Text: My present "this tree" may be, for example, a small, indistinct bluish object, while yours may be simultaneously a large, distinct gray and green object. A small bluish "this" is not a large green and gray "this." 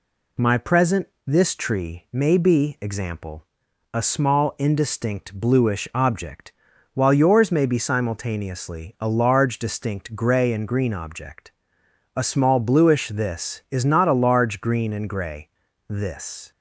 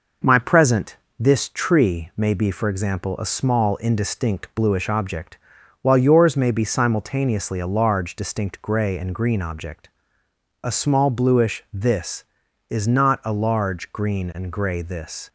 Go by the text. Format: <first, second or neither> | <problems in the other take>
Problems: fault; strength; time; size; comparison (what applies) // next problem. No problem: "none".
second | pauses between "present" and "this"; slight; at 1.0 s; 0.18 s long; slight in the second // skips "for"; at 2.7 s // pauses between "gray" and "this"; at 15.4 s; 0.41 s long